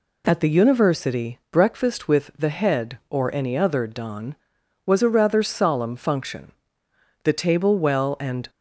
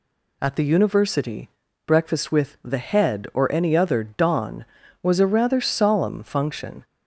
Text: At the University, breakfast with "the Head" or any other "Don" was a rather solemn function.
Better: second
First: goes on to say "The table well and"; noticeable; from 7.2 s on; 1.2 s long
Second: none

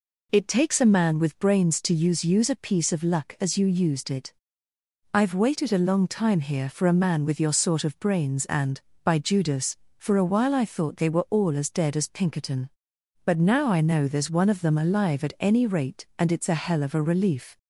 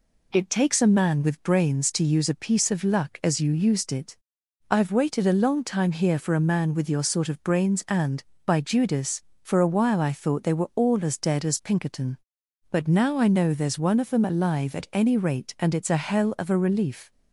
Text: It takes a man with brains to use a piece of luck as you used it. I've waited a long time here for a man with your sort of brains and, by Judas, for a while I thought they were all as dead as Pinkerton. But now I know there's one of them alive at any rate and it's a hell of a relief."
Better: second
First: says "use" twice; at 2.2 s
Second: none

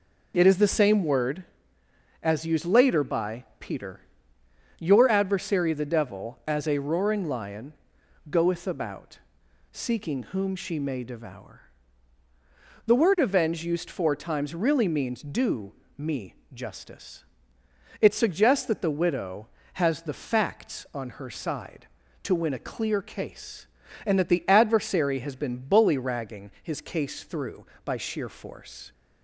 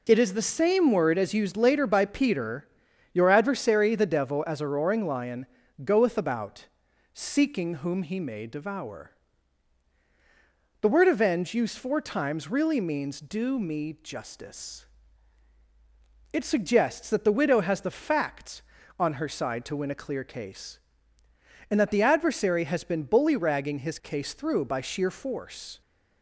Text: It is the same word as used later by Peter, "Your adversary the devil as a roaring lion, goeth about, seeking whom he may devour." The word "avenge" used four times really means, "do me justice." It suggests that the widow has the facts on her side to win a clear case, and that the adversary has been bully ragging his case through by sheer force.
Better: second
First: says "she" for "he"; at 10.5 s // pauses between "do" and "me"; slight; at 15.7 s; 0.24 s long // pauses between "me" and "justice"; slight; at 16.3 s; 0.20 s long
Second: none

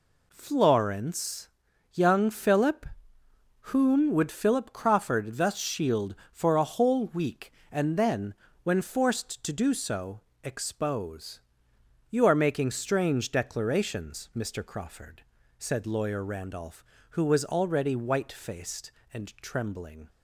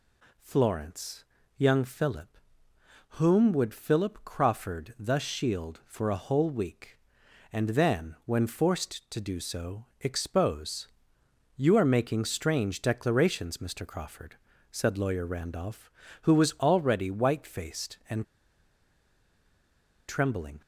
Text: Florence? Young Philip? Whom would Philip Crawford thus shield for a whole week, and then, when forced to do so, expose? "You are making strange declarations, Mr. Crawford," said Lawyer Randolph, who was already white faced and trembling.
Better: first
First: none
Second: pauses between "and" and "trembling"; strong; at 18.2 s; 1.8 s long

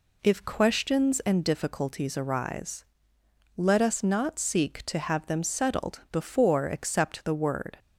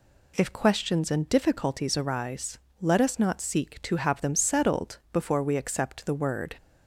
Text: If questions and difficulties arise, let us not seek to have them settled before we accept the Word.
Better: second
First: skips "we"; at 6.6 s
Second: none

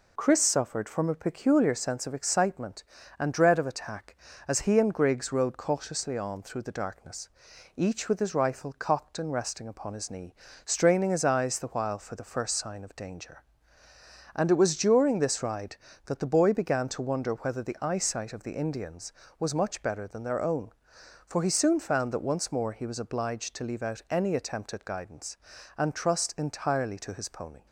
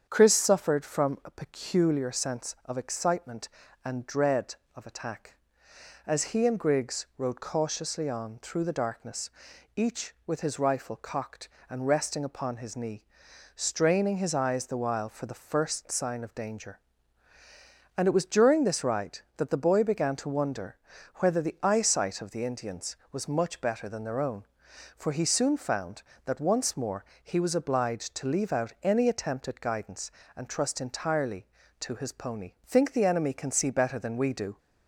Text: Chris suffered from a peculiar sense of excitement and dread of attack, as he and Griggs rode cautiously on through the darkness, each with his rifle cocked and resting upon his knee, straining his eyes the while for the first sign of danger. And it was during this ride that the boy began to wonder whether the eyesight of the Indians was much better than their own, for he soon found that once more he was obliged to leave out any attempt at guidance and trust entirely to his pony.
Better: first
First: none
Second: starts louder than the rest; strong; until 1.1 s; 8 dB // pauses between "wonder" and "whether"; at 20.7 s; 0.38 s long // pauses between "more" and "he"; slight; at 27.0 s; 0.20 s long // goes on to say "Think the enemy can see better than we do"; strong; from 32.6 s on; 1.9 s long

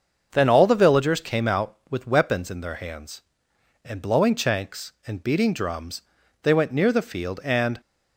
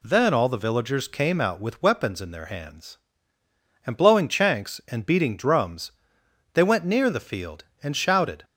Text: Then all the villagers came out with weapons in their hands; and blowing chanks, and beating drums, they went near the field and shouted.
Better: second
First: starts louder than the rest; until 1.3 s; 6.5 dB // stops before "shouted"; at 7.8 s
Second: none

